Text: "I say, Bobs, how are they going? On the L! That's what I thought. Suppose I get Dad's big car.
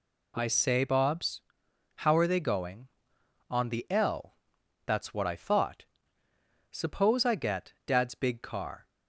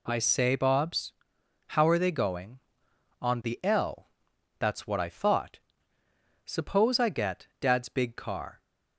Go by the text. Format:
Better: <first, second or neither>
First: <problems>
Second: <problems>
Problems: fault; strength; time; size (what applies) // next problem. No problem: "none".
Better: neither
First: none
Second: none